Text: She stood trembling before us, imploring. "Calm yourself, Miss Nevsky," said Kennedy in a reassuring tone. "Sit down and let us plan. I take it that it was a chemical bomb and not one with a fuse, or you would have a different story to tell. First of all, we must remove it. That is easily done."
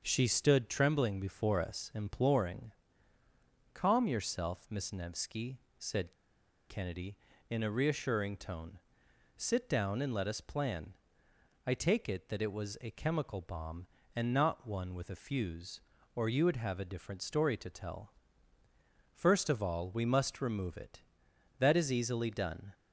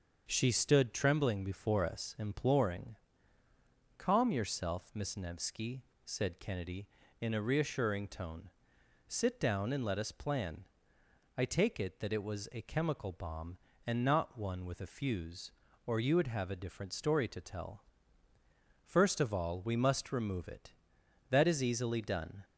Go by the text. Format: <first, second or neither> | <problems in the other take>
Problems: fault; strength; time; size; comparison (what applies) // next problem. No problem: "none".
second | starts louder than the rest; until 1.0 s; 6.5 dB; also in the second // pauses between "said" and "Kennedy"; noticeable; at 6.1 s; 0.58 s long